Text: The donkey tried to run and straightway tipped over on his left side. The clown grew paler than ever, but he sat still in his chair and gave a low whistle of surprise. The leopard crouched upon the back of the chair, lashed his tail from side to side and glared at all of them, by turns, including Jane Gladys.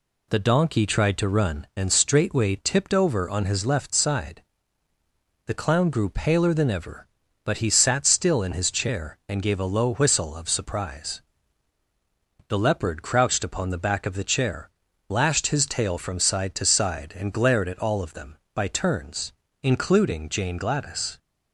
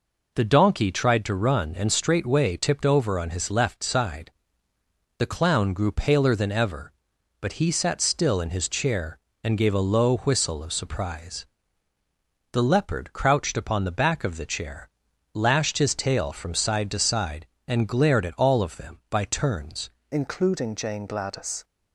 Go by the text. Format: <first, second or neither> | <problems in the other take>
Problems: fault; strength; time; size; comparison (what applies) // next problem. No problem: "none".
first | changes voice at "including"; from 20.1 s on; 1.5 s long